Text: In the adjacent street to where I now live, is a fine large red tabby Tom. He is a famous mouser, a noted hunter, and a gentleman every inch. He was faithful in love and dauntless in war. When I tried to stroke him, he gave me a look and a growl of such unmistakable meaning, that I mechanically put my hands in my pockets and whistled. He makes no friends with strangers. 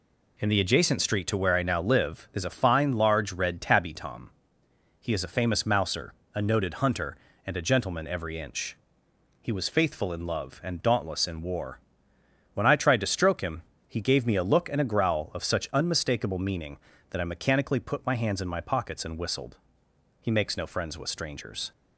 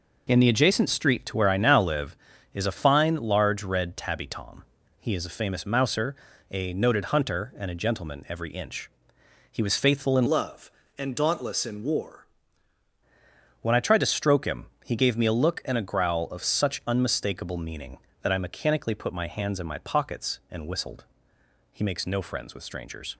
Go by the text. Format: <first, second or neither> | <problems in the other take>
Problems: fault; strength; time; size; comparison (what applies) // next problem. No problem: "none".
first | changes voice from "love" to "war"; from 10.2 to 12.2 s; 2.0 s long